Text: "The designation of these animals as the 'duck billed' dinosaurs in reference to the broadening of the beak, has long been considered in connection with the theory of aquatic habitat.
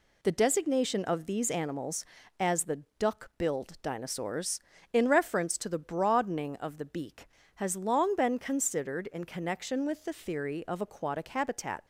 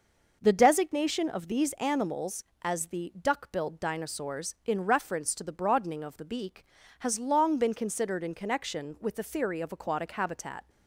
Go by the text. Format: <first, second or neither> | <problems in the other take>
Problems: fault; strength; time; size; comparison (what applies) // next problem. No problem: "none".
neither | none